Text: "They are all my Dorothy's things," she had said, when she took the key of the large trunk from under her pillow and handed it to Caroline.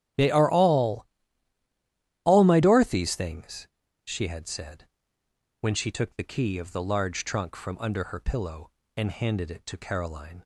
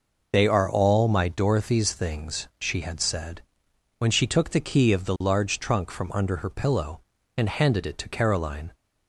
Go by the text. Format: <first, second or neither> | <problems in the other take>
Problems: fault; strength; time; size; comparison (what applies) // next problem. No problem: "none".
second | starts louder than the rest; strong; until 2.3 s; 11 dB // says "all" twice; at 2.2 s